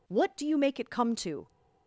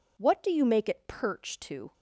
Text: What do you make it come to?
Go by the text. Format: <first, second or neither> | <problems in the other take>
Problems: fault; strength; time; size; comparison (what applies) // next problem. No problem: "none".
first | says "perch" for "come"; at 1.0 s